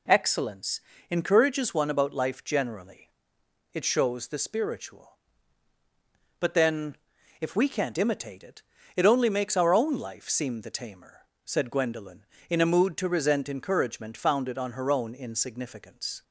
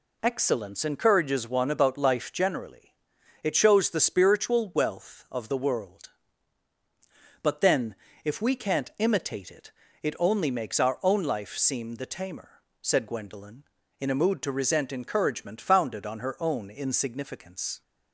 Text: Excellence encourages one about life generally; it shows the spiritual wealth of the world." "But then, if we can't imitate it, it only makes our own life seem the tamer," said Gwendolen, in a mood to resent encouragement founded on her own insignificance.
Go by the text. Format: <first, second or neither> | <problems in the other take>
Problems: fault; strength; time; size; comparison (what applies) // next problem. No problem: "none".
second | pauses between "Excellence" and "encourages"; slight; at 0.7 s; 0.32 s long // skips "wealth of the world"; at 5.7 s